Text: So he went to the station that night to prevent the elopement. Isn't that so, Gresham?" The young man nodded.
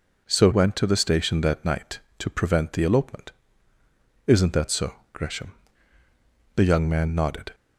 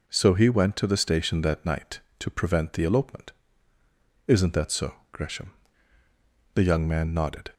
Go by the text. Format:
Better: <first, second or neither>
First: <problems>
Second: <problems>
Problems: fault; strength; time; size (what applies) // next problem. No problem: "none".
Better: second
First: skips "he"; at 0.5 s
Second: none